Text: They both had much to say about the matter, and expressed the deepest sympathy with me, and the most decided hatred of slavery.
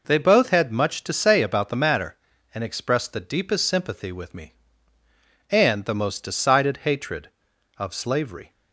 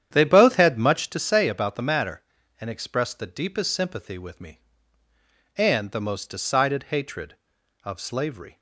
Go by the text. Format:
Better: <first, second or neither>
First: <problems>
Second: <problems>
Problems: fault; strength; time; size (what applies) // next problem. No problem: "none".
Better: first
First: none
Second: starts louder than the rest; strong; until 1.2 s; 9.5 dB